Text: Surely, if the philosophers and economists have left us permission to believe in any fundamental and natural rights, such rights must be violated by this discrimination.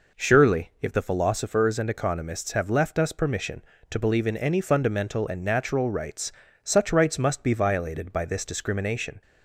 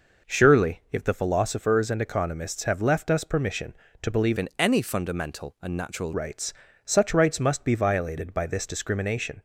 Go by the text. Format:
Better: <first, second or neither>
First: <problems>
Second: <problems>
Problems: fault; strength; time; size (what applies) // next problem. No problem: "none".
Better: first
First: none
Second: changes voice from "in" to "natural"; from 4.3 to 6.1 s; 1.8 s long